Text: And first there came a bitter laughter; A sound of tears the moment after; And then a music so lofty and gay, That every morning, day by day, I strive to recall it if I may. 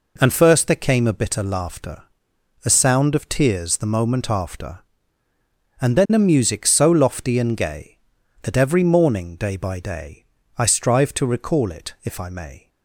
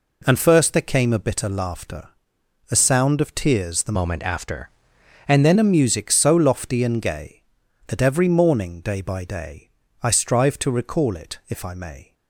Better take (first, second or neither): first